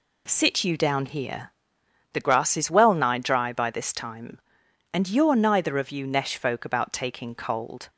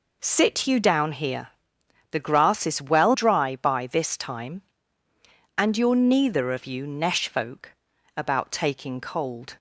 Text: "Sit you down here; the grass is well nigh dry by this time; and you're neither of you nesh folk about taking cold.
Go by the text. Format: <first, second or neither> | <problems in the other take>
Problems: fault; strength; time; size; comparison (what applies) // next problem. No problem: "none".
first | skips "nigh"; at 3.1 s // pauses between "folk" and "about"; noticeable; at 7.7 s; 0.46 s long